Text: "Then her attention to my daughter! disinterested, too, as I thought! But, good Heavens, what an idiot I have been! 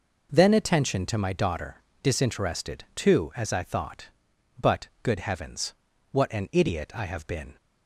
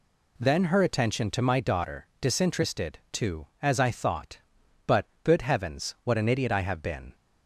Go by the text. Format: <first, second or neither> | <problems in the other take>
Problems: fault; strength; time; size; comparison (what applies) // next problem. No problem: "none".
second | skips "her"; at 0.5 s